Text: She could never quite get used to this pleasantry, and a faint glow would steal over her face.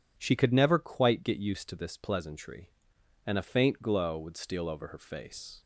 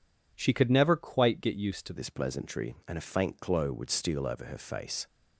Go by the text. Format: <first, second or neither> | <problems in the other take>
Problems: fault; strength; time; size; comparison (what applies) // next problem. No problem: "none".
first | changes voice at "this"; from 1.9 s on; 3.1 s long